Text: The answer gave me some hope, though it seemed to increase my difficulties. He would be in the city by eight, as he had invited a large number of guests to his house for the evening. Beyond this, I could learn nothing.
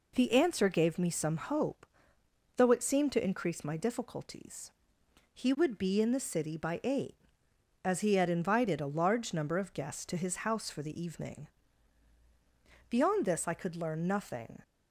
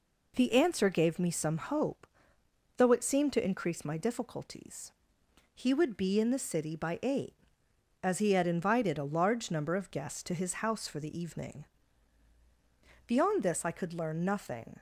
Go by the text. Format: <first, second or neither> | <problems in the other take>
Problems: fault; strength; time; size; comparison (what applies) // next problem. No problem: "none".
neither | none